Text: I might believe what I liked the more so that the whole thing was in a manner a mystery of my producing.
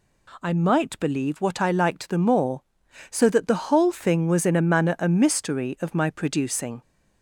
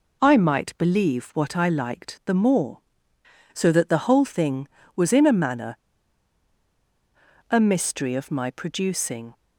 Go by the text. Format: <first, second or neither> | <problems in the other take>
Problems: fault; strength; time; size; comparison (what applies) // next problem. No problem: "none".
first | pauses between "manner" and "a"; strong; at 5.7 s; 1.7 s long